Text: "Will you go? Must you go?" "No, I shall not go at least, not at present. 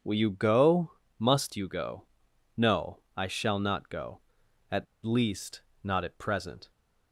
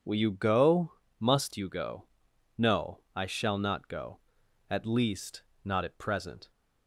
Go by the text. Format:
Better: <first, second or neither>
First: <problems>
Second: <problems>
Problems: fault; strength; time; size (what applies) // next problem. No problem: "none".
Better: second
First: pauses between "at" and "least"; slight; at 4.8 s; 0.20 s long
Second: none